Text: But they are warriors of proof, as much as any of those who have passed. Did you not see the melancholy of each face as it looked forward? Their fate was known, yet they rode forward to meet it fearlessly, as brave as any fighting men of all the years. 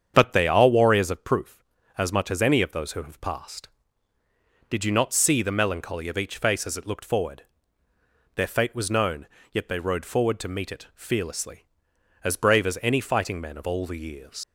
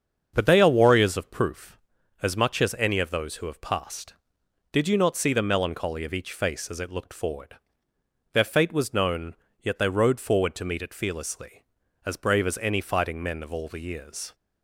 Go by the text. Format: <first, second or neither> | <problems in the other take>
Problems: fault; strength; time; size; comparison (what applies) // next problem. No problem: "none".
second | starts louder than the rest; strong; until 1.1 s; 8 dB; also in the second // leaves "years" unfinished; at 14.4 s; 75 ms